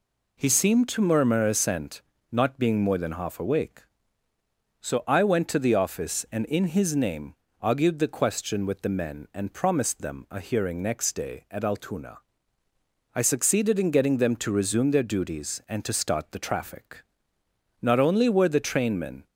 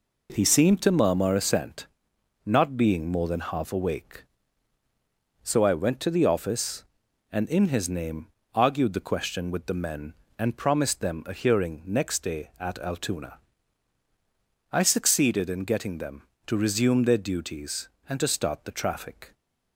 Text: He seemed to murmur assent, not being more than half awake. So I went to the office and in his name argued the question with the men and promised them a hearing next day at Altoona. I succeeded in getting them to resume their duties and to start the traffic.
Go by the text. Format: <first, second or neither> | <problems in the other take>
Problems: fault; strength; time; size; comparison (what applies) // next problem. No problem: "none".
second | pauses between "name" and "argued"; slight; at 7.3 s; 0.26 s long; slight in the second // goes on to say "Not only were the trainmen"; from 17.8 s on; 1.4 s long